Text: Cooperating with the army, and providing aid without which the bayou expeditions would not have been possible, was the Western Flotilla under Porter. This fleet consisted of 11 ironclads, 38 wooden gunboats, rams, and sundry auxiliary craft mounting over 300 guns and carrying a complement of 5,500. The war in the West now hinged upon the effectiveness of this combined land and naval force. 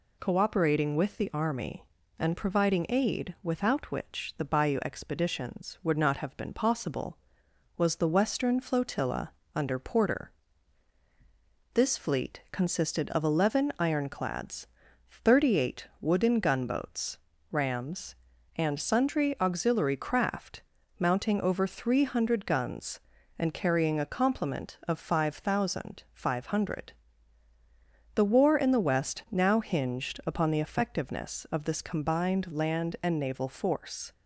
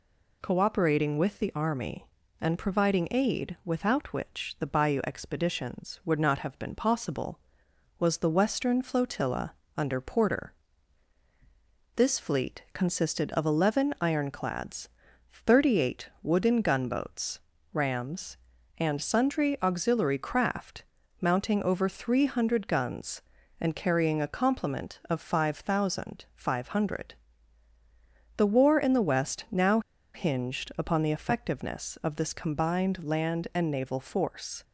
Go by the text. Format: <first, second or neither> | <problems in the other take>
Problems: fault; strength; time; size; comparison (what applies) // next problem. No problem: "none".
first | pauses between "Flotilla" and "under"; slight; at 9.5 s; 0.22 s long; slight in the first // pauses between "craft" and "mounting"; slight; at 20.8 s; 0.36 s long; slight in the first // pauses between "now" and "hinged"; slight; at 29.7 s; 0.34 s long